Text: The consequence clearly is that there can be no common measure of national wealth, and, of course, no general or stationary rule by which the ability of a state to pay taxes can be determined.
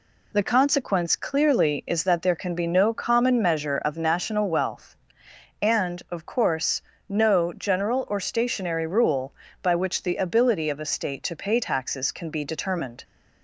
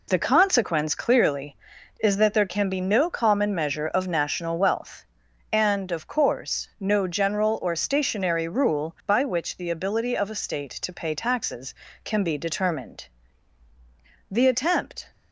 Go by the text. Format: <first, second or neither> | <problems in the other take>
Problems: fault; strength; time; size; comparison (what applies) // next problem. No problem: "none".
first | goes on to say "The attempt"; noticeable; from 14.3 s on; 0.80 s long